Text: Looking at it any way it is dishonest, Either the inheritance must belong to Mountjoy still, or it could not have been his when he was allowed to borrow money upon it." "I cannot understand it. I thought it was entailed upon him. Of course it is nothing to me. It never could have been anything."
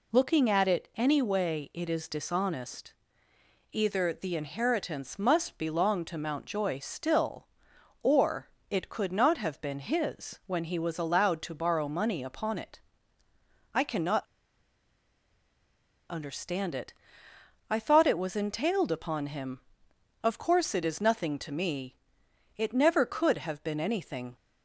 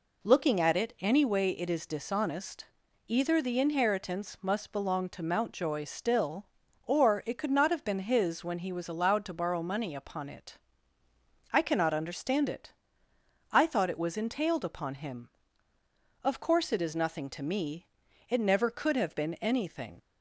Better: second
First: pauses between "or" and "it"; slight; at 8.4 s; 0.20 s long // pauses between "cannot" and "understand"; strong; at 14.2 s; 1.8 s long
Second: none

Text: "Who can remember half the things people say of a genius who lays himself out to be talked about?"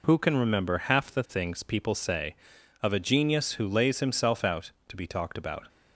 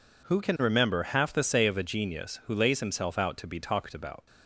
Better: first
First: none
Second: skips "things people"; at 1.4 s

